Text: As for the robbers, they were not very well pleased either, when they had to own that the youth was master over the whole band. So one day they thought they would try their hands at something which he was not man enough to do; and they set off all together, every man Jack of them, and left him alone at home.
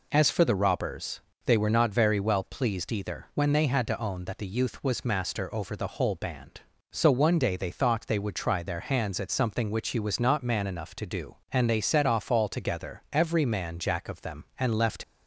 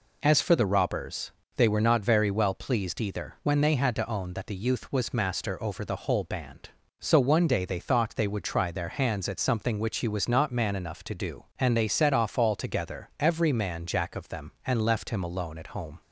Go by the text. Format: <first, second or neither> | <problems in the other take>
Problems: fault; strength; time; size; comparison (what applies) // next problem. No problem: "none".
second | stops before "him alone at home"; at 15.0 s